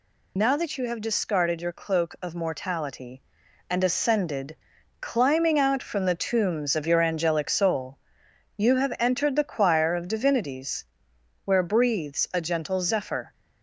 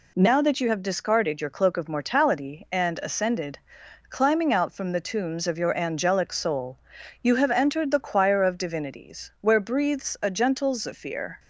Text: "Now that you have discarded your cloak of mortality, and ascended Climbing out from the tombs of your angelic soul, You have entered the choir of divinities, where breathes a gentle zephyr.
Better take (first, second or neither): second